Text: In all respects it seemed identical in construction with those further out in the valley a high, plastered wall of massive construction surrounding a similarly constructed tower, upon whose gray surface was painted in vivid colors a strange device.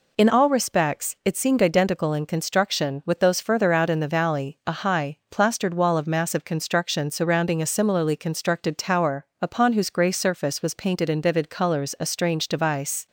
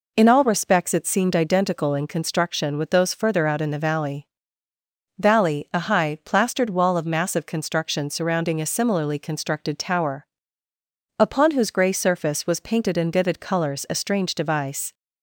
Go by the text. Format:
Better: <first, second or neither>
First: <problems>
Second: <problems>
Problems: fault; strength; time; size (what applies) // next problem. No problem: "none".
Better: first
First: none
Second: says "valley" twice; at 5.1 s